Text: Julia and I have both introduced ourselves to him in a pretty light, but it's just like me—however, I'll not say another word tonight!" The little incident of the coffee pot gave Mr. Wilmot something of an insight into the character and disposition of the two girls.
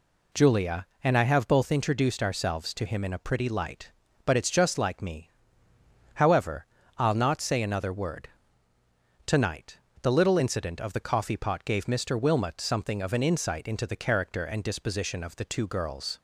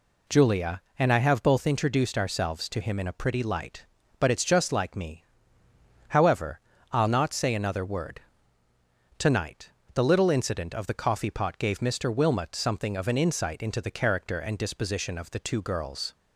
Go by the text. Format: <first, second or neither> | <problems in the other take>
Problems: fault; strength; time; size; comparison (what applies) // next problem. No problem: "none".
neither | pauses between "word" and "tonight"; noticeable; the same in both